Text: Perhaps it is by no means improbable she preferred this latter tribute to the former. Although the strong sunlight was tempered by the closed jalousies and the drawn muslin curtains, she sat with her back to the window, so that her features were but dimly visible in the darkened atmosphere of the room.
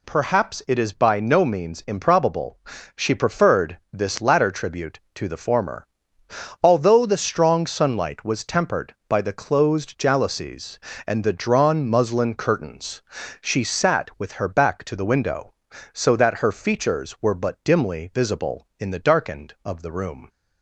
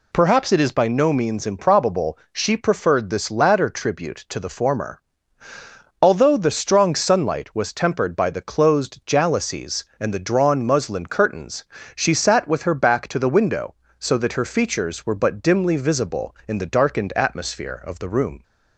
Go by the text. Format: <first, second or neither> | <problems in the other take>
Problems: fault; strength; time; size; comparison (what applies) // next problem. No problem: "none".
second | pauses between "improbable" and "she"; slight; at 2.5 s; 0.36 s long; slight in the second // skips "atmosphere"; at 19.5 s